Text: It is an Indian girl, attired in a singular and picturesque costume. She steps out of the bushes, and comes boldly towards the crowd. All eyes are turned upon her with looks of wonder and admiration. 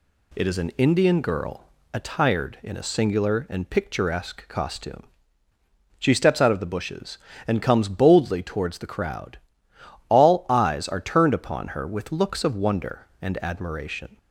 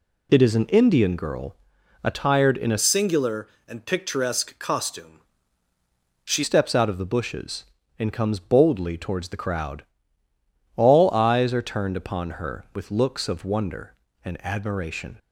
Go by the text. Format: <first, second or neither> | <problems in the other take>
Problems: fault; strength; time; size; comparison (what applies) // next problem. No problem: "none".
first | changes voice from "singular" to "She"; from 2.7 to 6.4 s; 3.7 s long